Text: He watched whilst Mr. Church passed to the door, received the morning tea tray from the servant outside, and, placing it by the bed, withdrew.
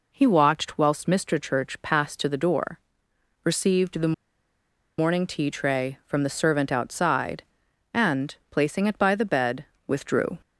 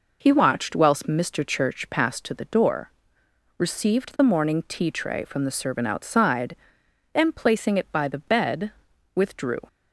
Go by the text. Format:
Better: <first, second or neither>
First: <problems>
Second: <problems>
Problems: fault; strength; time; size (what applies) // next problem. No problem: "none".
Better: second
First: pauses between "the" and "morning"; noticeable; at 4.1 s; 0.84 s long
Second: none